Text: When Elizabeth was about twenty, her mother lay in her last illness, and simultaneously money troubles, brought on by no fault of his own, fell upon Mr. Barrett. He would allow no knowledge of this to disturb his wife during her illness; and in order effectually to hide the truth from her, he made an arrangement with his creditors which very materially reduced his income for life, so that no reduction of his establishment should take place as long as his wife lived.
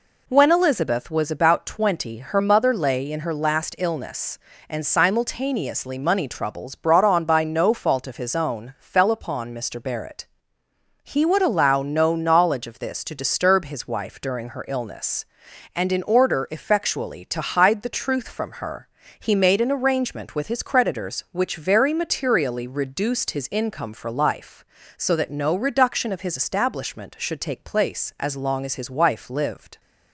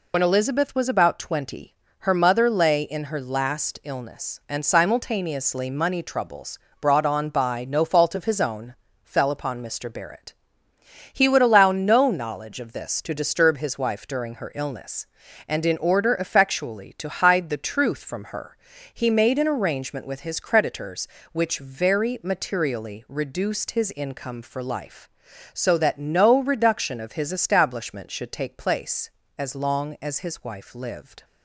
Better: first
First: none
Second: loses the start of "When"; at 0.1 s; 50 ms

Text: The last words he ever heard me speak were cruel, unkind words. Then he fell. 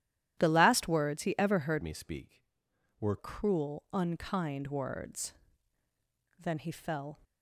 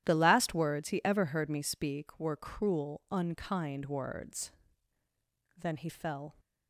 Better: second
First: starts louder than the rest; strong; until 1.4 s; 12 dB // changes voice from "me" to "were"; from 1.8 to 3.1 s; 1.3 s long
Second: starts louder than the rest; strong; until 1.0 s; 11.5 dB

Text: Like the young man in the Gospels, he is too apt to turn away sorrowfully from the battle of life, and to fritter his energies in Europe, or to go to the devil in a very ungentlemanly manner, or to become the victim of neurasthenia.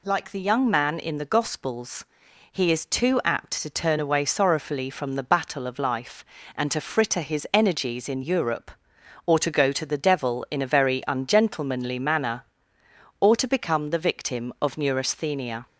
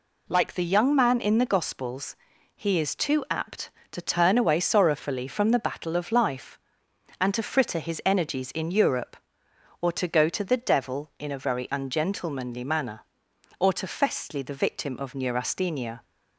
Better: first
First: none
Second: says "festly" for "become"; at 13.8 s

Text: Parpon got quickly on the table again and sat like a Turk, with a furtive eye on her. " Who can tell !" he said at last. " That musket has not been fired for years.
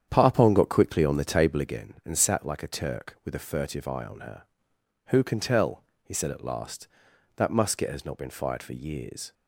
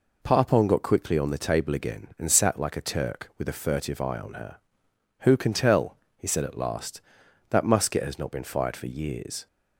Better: second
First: starts louder than the rest; strong; until 1.7 s; 9 dB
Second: none

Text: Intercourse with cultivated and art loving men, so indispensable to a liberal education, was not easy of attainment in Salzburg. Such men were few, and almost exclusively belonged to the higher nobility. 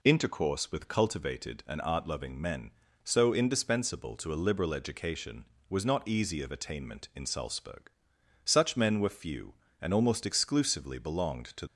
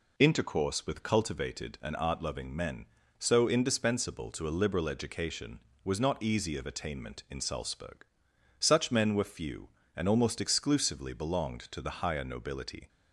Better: second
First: stops before "the higher nobility"; at 11.6 s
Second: none

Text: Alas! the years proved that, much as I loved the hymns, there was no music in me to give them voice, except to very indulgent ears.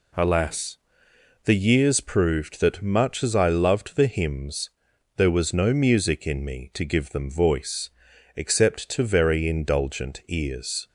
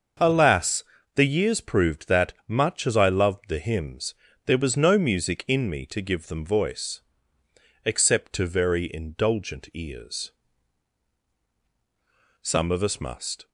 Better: first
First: none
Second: starts louder than the rest; until 1.5 s; 6.5 dB // goes on to say "Some of us must"; noticeable; from 12.4 s on; 1.0 s long

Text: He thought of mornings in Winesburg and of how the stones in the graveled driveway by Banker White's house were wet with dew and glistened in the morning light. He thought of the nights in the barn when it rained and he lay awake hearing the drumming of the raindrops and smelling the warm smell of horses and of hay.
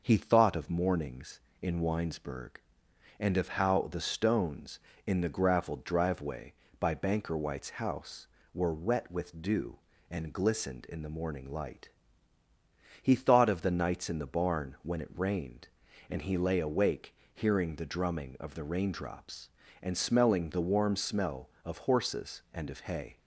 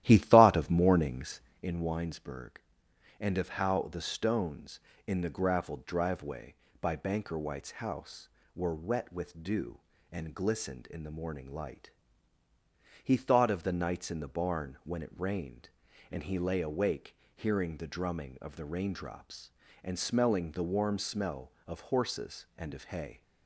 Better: first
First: pauses between "awake" and "hearing"; slight; at 17.1 s; 0.18 s long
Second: starts louder than the rest; strong; until 1.7 s; 13 dB // pauses between "awake" and "hearing"; slight; at 17.1 s; 0.18 s long

